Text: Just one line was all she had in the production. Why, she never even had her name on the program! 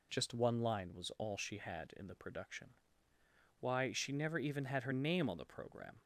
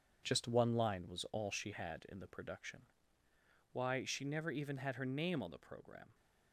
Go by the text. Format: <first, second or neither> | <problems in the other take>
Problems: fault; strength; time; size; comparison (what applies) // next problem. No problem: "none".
first | gets quieter; strong; throughout; 8 dB